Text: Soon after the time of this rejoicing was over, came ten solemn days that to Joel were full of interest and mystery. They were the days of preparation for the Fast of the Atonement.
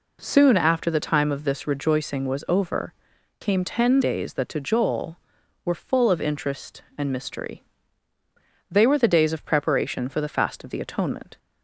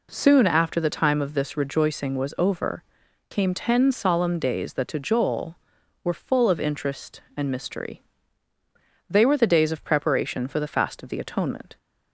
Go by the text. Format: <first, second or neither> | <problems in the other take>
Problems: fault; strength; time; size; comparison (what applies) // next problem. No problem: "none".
second | skips "solemn"; at 4.0 s